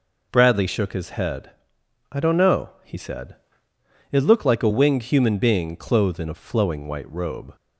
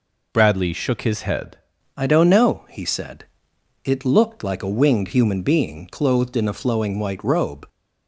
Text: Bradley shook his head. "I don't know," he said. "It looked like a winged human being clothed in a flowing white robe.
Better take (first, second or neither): first